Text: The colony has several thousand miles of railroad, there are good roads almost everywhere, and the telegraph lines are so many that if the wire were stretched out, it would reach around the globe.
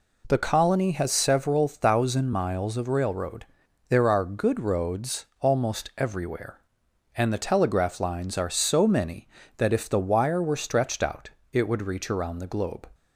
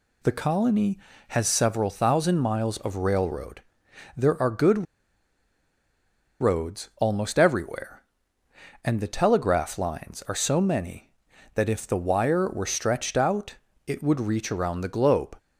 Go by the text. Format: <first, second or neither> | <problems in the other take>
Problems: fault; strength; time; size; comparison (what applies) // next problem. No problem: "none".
first | pauses between "good" and "roads"; strong; at 4.8 s; 1.5 s long